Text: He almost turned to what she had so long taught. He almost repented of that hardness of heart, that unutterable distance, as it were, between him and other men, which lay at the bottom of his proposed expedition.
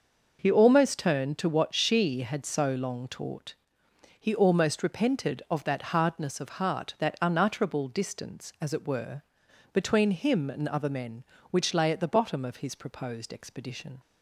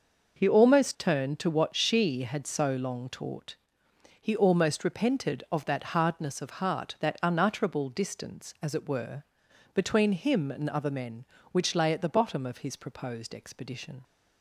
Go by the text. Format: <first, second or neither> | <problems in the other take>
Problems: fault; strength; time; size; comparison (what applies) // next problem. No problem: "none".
neither | starts louder than the rest; noticeable; the same in both